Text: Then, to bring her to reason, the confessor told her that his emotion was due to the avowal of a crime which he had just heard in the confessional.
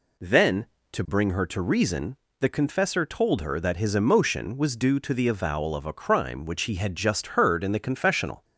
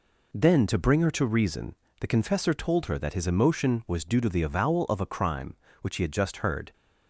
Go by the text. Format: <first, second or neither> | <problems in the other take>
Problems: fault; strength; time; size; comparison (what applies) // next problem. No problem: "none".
first | stops before "in the confessional"; at 6.7 s